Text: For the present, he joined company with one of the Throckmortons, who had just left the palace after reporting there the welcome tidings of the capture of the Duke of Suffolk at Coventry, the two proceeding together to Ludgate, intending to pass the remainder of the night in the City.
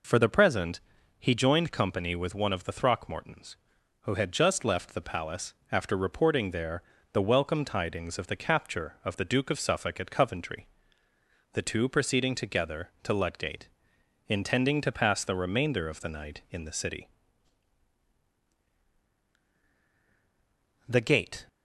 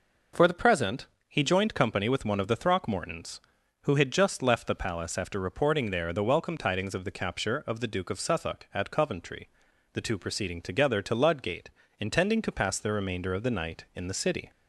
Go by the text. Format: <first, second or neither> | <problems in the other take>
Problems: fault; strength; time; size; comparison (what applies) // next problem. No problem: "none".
second | pauses between "palace" and "after"; slight; at 5.5 s; 0.18 s long // pauses between "there" and "the"; slight; at 6.8 s; 0.28 s long // goes on to say "The gate"; from 20.8 s on; 0.60 s long